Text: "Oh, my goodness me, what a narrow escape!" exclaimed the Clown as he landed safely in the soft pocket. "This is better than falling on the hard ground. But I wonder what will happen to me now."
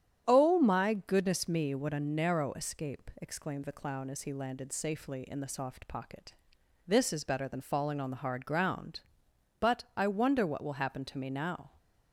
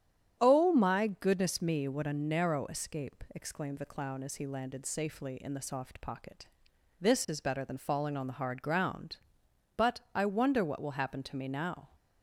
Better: neither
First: starts louder than the rest; strong; until 1.2 s; 9.5 dB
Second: starts louder than the rest; strong; until 1.4 s; 9.5 dB

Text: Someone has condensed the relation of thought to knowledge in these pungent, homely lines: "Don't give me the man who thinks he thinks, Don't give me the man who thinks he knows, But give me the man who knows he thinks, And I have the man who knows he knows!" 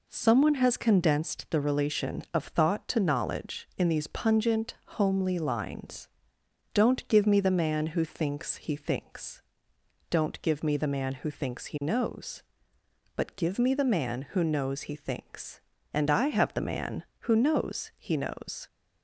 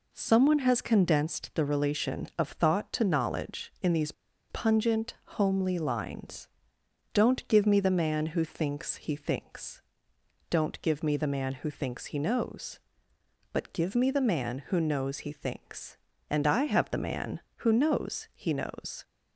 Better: first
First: none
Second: pauses between "these" and "pungent"; at 4.1 s; 0.38 s long

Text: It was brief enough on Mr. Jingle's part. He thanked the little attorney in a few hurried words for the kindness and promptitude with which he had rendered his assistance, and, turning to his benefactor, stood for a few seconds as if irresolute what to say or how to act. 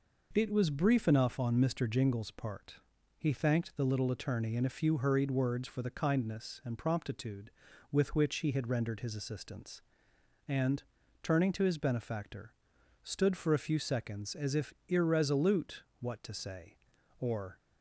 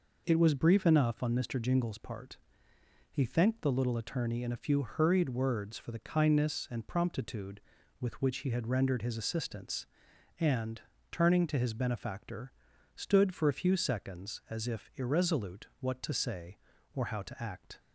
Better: second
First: pauses between "if" and "irresolute"; slight; at 14.7 s; 0.16 s long // pauses between "irresolute" and "what"; slight; at 15.8 s; 0.16 s long // stops before "how to act"; at 17.5 s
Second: none

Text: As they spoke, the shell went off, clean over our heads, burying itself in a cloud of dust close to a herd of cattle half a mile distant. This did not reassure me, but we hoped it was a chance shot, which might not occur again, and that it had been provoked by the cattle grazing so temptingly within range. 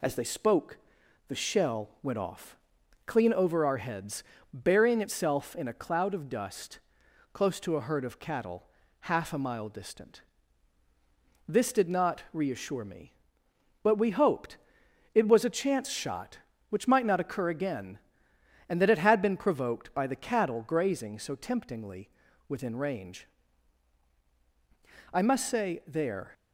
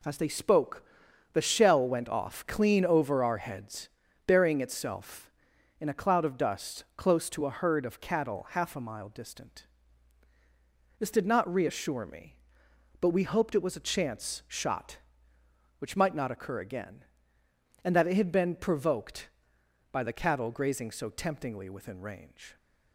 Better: second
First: pauses between "dust" and "close"; noticeable; at 6.7 s; 0.54 s long // pauses between "cattle" and "half"; slight; at 8.6 s; 0.34 s long // pauses between "hoped" and "it"; noticeable; at 14.5 s; 0.56 s long // pauses between "temptingly" and "within"; at 22.0 s; 0.38 s long // goes on to say "I must say there"; noticeable; from 25.1 s on; 1.1 s long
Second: none

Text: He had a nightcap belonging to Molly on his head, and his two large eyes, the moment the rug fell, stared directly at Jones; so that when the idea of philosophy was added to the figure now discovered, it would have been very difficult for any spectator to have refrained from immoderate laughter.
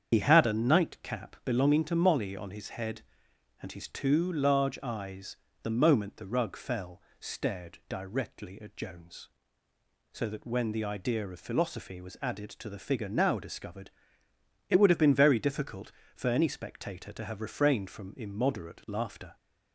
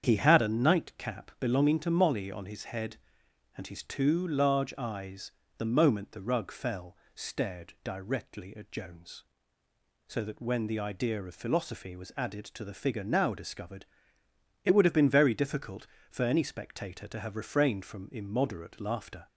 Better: second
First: loses the start of "He"; at 0.1 s; 55 ms // starts louder than the rest; strong; until 1.1 s; 8 dB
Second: starts louder than the rest; strong; until 1.0 s; 8 dB

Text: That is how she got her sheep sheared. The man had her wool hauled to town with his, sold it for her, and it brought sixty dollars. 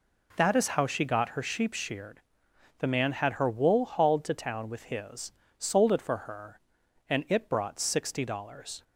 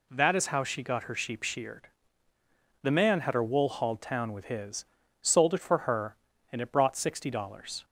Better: first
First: none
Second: skips "to"; at 4.0 s

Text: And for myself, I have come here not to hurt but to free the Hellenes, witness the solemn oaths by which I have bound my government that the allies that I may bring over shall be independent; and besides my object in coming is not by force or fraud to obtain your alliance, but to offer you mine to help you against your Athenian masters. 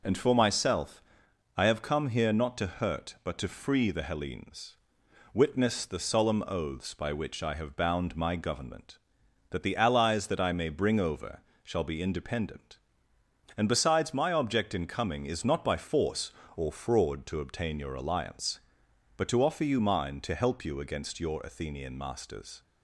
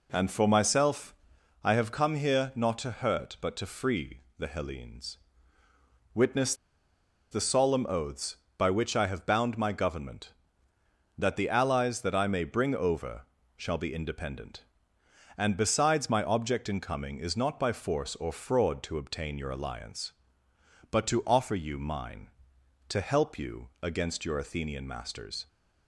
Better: first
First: pauses between "over" and "shall"; slight; at 11.4 s; 0.22 s long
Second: pauses between "free" and "the"; slight; at 4.2 s; 0.18 s long // pauses between "witness" and "the"; noticeable; at 6.5 s; 0.76 s long // pauses between "over" and "shall"; slight; at 13.2 s; 0.36 s long

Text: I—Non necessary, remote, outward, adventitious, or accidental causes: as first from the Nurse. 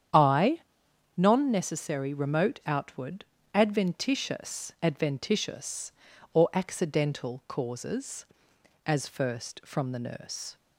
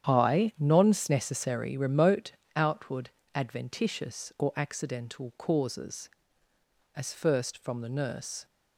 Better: second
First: starts louder than the rest; strong; until 1.6 s; 9 dB // says "adventitious" twice; at 4.8 s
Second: starts louder than the rest; strong; until 1.1 s; 9 dB

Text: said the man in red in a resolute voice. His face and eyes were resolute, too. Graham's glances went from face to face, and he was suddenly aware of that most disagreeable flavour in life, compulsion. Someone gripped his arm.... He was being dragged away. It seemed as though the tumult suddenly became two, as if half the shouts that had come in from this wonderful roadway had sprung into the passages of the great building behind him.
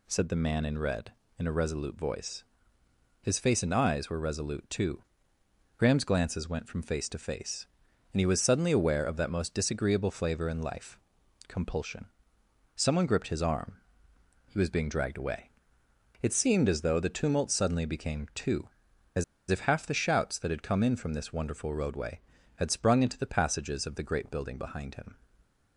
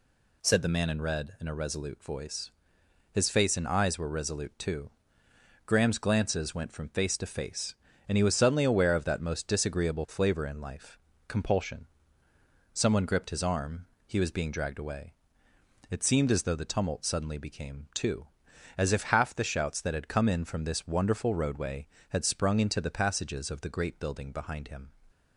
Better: second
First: pauses between "as" and "if"; slight; at 19.2 s; 0.26 s long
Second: none

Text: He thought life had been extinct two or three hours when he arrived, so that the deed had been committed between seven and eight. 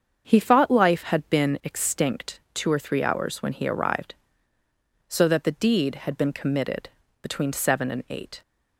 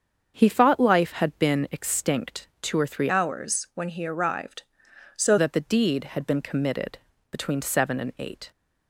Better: first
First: starts louder than the rest; until 1.2 s; 7 dB // pauses between "committed" and "between"; slight; at 6.8 s; 0.32 s long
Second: starts louder than the rest; until 1.3 s; 7 dB // changes voice from "hours" to "so"; from 3.0 to 5.3 s; 2.3 s long // pauses between "committed" and "between"; slight; at 6.9 s; 0.32 s long

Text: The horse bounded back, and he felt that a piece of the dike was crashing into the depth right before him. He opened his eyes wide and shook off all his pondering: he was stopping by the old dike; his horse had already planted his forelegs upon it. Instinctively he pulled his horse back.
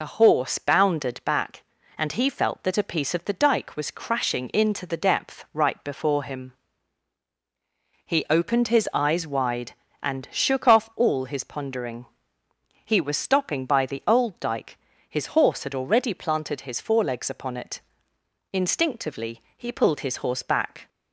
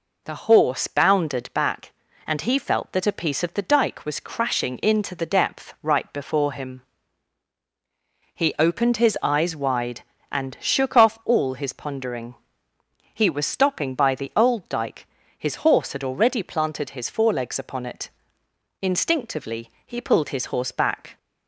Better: second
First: loses the start of "The"; at 0.0 s; 40 ms // pauses between "Instinctively" and "he"; slight; at 19.4 s; 0.16 s long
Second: pauses between "Instinctively" and "he"; slight; at 19.6 s; 0.16 s long

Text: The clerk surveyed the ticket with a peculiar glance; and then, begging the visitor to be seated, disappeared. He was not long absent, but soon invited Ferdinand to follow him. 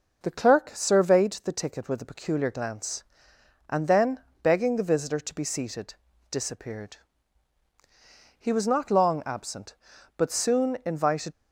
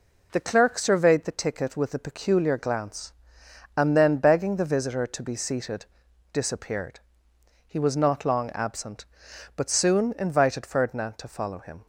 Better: second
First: starts louder than the rest; noticeable; until 1.2 s; 6 dB // stops before "Ferdinand to follow him"; at 11.3 s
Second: none

